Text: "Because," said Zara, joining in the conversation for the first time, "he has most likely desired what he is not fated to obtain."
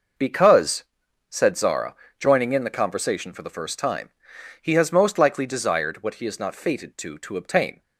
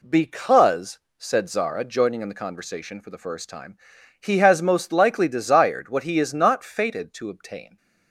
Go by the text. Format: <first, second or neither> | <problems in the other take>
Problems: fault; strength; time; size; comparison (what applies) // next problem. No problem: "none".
second | says "to" twice; at 7.1 s